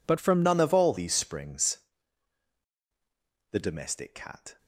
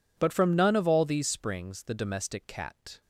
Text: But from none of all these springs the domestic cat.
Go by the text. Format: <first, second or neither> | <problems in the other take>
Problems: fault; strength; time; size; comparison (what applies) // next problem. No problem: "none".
second | changes voice at "none"; from 0.4 s on; 4.1 s long // pauses between "springs" and "the"; strong; at 1.7 s; 1.7 s long